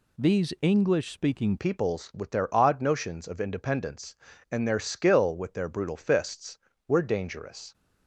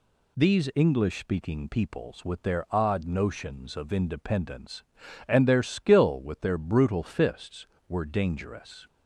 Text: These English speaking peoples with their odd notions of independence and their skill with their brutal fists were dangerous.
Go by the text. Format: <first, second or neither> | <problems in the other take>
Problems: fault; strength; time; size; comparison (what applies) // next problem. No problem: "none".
second | changes voice at "peoples"; from 1.5 s on; 6.2 s long